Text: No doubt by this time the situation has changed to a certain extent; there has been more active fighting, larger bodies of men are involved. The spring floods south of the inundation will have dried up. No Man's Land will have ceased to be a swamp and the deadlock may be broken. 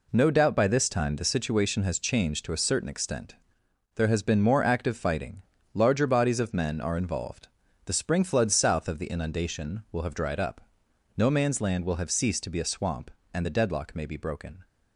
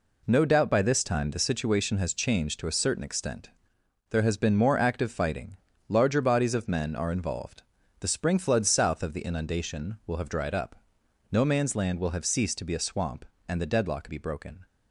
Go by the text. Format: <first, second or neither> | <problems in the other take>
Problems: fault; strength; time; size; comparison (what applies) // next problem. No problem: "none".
first | skips "may"; at 14.0 s